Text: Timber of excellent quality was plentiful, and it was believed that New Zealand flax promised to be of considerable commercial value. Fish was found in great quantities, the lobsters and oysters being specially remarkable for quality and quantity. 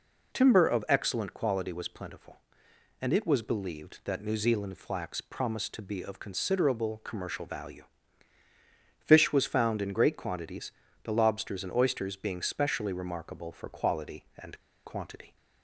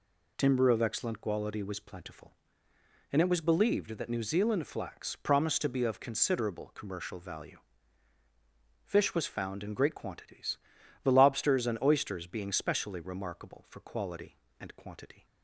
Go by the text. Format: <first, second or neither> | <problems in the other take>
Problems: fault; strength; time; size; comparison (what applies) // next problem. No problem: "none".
second | pauses between "and" and "quantity"; slight; at 14.5 s; 0.28 s long